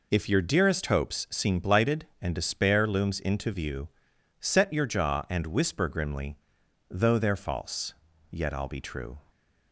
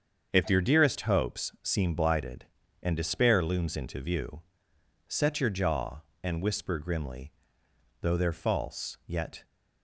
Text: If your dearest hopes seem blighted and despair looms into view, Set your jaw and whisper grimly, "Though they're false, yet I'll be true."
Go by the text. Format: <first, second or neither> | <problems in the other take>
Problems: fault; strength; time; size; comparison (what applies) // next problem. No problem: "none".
first | starts louder than the rest; until 1.3 s; 7 dB // stops before "I'll be true"; at 9.4 s